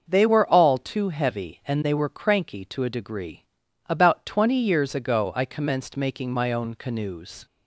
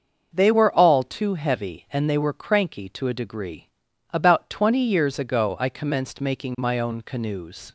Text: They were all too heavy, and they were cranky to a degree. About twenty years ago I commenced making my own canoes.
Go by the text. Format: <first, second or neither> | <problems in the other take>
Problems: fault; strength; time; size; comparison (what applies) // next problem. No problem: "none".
neither | starts louder than the rest; the same in both